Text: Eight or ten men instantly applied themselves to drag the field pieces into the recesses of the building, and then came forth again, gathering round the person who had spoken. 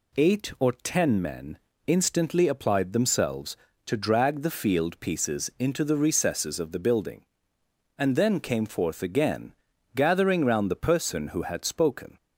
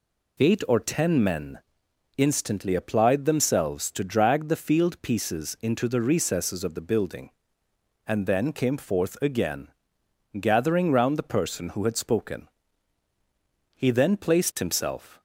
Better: first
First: pauses between "men" and "instantly"; slight; at 1.5 s; 0.30 s long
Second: pauses between "men" and "instantly"; noticeable; at 1.5 s; 0.58 s long // goes on to say "He then placed himself"; from 13.7 s on; 1.4 s long

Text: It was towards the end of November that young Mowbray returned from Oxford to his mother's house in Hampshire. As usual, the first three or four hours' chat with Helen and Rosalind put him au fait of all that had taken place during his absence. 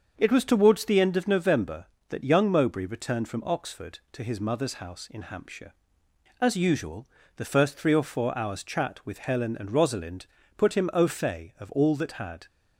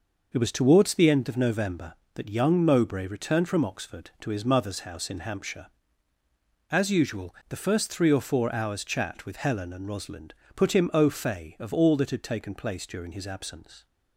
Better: second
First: starts louder than the rest; until 1.1 s; 6.5 dB // pauses between "Rosalind" and "put"; slight; at 10.2 s; 0.30 s long // stops before "taken place during his absence"; at 12.4 s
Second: pauses between "Rosalind" and "put"; slight; at 10.3 s; 0.20 s long

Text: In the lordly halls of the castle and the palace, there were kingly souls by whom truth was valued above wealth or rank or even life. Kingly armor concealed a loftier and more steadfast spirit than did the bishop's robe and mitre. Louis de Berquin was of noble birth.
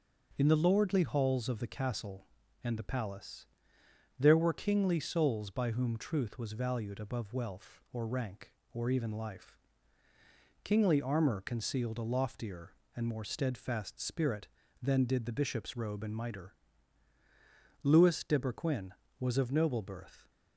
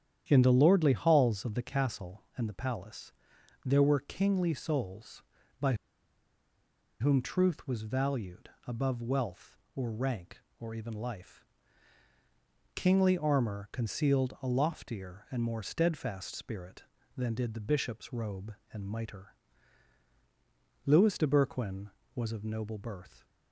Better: first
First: starts louder than the rest; until 1.3 s; 6 dB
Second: starts louder than the rest; strong; until 1.2 s; 9.5 dB // pauses between "by" and "whom"; strong; at 5.7 s; 1.2 s long // pauses between "valued" and "above"; slight; at 8.4 s; 0.20 s long

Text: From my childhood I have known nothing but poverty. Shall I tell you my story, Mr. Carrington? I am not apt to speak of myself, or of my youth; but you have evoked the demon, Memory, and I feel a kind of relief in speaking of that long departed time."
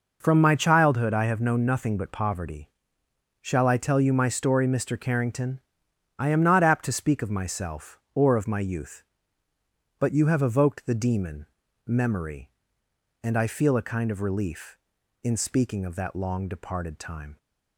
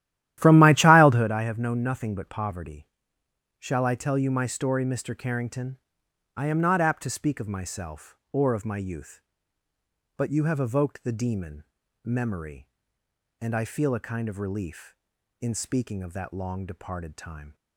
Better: first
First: none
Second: starts louder than the rest; strong; until 1.3 s; 13 dB

